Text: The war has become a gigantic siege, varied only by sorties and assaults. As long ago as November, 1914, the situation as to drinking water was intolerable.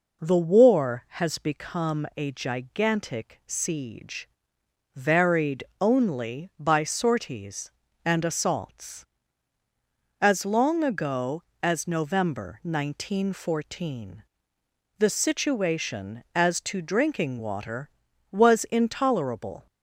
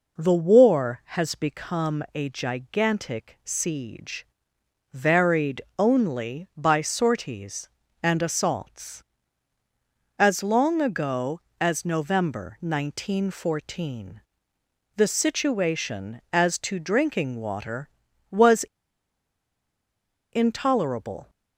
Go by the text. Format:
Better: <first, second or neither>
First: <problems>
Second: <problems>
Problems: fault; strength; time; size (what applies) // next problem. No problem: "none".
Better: first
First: pauses between "varied" and "only"; slight; at 5.6 s; 0.18 s long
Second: pauses between "varied" and "only"; slight; at 5.5 s; 0.18 s long // pauses between "was" and "intolerable"; strong; at 18.6 s; 1.7 s long